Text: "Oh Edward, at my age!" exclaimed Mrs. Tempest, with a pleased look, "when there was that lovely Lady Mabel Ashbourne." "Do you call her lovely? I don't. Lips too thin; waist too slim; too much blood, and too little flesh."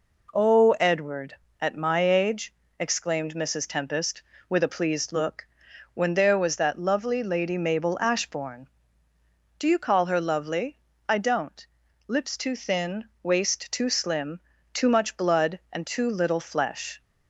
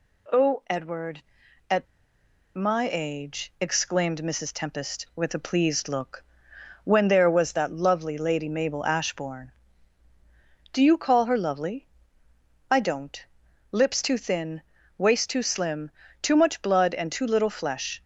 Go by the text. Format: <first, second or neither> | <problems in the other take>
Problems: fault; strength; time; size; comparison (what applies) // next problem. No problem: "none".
first | pauses between "at" and "my"; noticeable; at 1.8 s; 0.71 s long